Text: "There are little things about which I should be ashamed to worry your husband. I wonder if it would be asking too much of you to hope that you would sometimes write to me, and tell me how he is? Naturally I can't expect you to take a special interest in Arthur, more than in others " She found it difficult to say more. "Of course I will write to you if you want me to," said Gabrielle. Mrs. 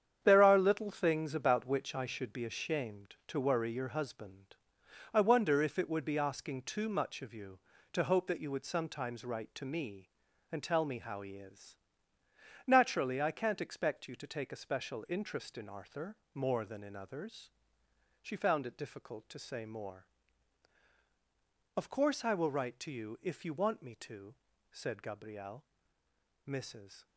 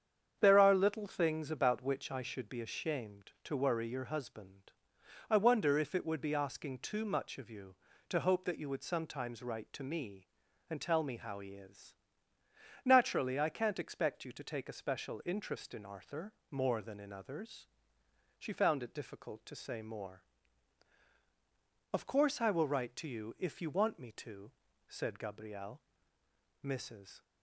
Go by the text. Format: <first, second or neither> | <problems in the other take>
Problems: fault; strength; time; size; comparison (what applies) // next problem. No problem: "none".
second | gets quieter; strong; throughout; 10.5 dB // starts louder than the rest; strong; until 1.2 s; 8.5 dB; strong in the second